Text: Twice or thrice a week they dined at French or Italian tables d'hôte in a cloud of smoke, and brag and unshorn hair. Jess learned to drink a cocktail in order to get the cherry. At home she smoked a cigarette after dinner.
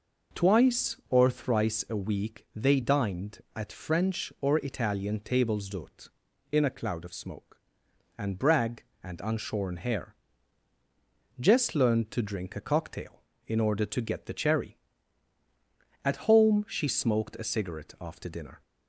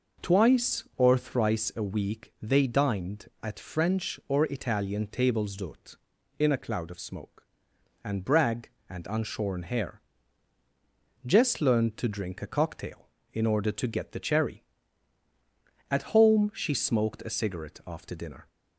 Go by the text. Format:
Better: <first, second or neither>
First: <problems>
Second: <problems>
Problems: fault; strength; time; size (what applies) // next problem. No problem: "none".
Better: neither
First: none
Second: none